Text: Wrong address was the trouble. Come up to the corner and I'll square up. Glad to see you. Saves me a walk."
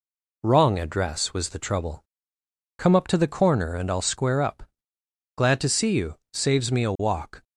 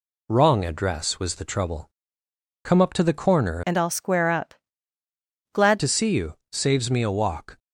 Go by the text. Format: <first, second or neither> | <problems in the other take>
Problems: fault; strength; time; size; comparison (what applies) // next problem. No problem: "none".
first | changes voice from "and" to "Glad"; from 3.6 to 5.7 s; 2.1 s long